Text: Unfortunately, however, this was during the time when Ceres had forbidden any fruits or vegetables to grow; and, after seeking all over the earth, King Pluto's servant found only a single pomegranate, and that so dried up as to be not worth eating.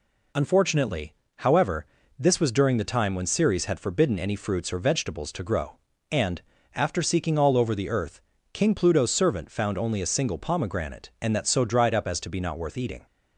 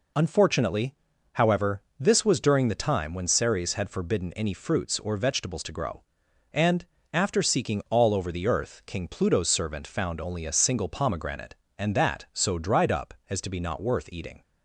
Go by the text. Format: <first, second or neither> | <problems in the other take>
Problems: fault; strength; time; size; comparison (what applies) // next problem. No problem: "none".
neither | none